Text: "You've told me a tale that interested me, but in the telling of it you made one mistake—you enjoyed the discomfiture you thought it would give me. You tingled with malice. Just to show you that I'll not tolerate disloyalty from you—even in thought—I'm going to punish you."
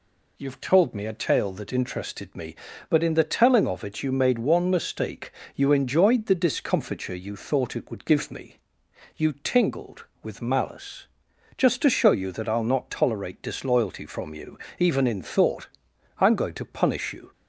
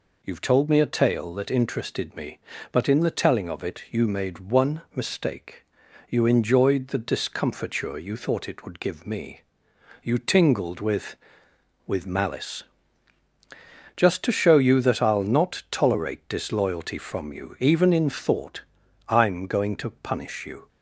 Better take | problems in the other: first | says "with" twice; at 11.8 s

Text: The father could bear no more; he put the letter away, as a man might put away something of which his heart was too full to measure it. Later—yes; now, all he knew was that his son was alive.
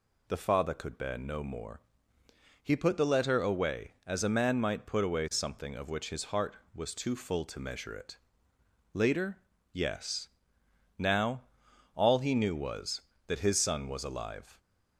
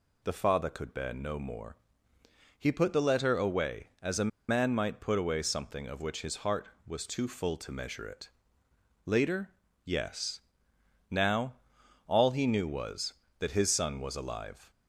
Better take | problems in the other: first | pauses between "a" and "man"; slight; at 4.3 s; 0.18 s long

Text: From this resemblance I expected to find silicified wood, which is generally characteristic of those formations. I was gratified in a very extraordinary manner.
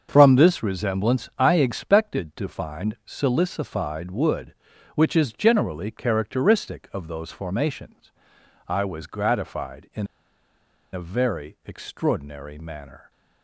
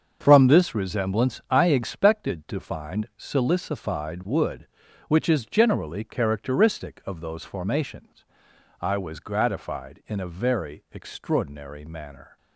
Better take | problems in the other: second | starts louder than the rest; until 1.1 s; 6.5 dB; also in the second // pauses between "in" and "a"; noticeable; at 10.0 s; 0.87 s long

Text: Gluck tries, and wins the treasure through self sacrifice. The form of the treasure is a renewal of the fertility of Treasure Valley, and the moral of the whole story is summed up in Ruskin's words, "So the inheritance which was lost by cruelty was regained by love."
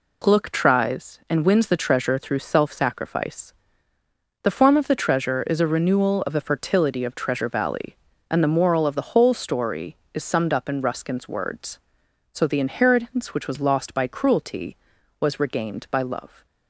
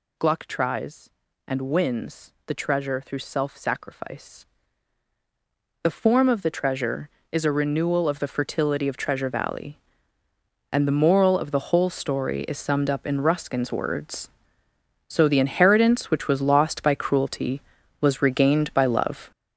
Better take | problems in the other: first | gets louder; strong; throughout; 8 dB

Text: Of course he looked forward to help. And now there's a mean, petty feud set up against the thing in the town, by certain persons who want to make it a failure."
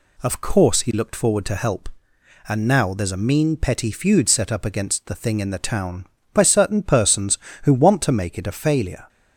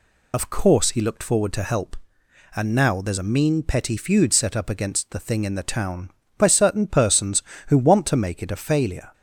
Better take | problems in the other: first | loses the start of "Of"; at 0.3 s; 60 ms

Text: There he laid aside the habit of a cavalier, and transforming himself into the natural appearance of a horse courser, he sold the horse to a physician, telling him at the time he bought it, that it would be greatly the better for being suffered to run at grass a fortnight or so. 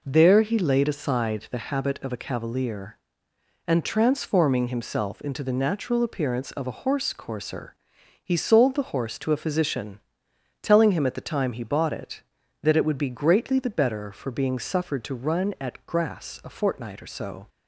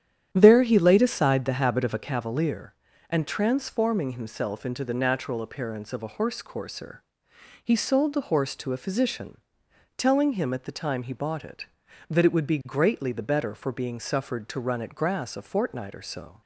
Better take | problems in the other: first | starts louder than the rest; strong; until 2.2 s; 10 dB

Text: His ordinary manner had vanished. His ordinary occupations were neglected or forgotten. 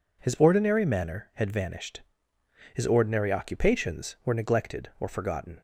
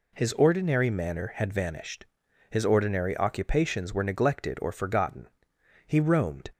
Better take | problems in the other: first | goes on to say "He roamed"; noticeable; from 5.8 s on; 0.64 s long

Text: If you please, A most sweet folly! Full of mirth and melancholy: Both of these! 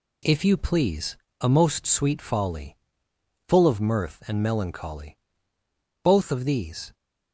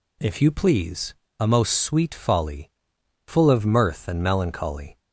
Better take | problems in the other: first | stops before "Both of these"; at 4.9 s

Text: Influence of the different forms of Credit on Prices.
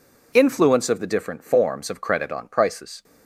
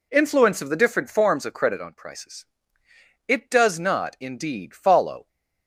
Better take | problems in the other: first | goes on to say "It does not indeed follow"; strong; from 3.2 s on; 2.0 s long

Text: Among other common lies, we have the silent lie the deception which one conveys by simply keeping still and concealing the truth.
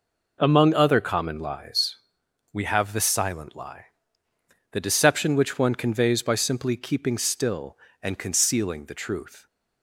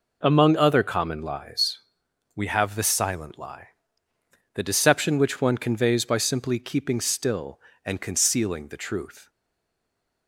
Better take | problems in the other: first | pauses between "lie" and "the"; noticeable; at 3.6 s; 0.84 s long; noticeable in the first // stays silent after the last word; from 9.2 s on; 1.0 s long

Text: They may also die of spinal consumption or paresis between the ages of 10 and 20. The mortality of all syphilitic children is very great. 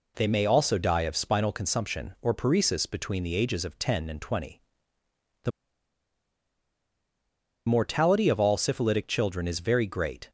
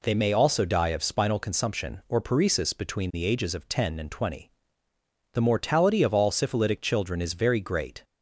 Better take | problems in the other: second | pauses between "The" and "mortality"; strong; at 5.5 s; 2.1 s long

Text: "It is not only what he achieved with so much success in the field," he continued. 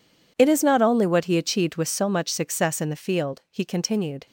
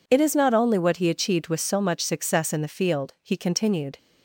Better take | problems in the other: second | gets quieter; strong; throughout; 16.5 dB

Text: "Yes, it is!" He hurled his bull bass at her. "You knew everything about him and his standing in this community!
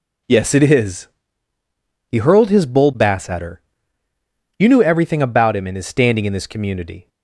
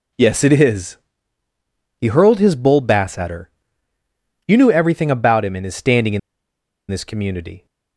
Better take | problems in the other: first | pauses between "in" and "this"; noticeable; at 6.1 s; 0.69 s long

